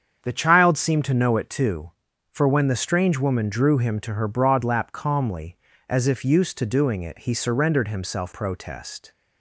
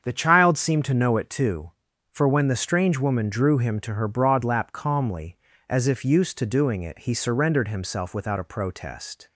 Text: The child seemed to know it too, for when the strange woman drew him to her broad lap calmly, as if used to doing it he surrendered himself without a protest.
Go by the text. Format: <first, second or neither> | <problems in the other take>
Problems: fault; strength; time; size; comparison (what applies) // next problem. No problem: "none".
second | starts louder than the rest; strong; until 1.2 s; 7.5 dB; strong in the second // skips "without a"; at 8.3 s